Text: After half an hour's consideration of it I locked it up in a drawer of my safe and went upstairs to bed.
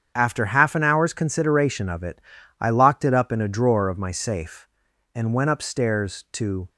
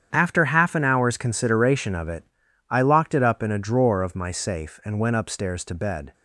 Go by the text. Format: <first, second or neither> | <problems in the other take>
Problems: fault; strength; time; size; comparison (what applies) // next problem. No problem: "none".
second | starts louder than the rest; strong; until 1.1 s; 7.5 dB; strong in the second // pauses between "it" and "I"; at 2.2 s; 0.38 s long; also in the second // stops before "bed"; at 6.6 s